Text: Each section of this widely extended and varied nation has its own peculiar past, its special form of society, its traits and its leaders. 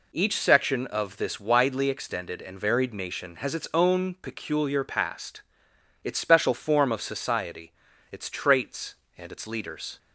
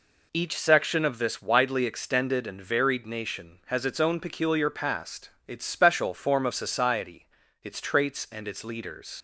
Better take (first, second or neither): first